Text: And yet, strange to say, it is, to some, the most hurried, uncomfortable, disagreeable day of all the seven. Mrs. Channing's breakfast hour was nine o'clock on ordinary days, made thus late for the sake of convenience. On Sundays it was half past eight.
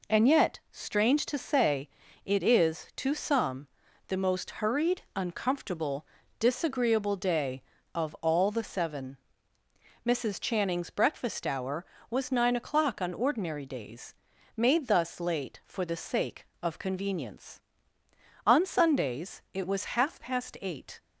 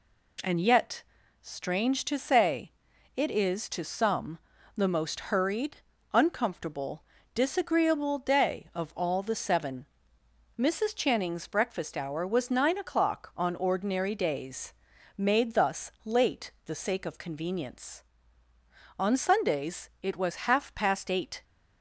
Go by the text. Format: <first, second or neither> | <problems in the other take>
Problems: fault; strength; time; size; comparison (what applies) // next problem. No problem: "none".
first | skips "for"; at 16.5 s